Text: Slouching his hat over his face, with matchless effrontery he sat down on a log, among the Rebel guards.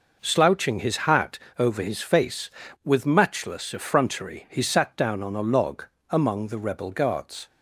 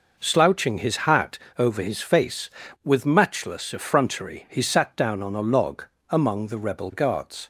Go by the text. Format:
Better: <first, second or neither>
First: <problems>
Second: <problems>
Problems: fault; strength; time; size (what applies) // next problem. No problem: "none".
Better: neither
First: pauses between "hat" and "over"; slight; at 1.3 s; 0.22 s long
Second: pauses between "hat" and "over"; slight; at 1.3 s; 0.22 s long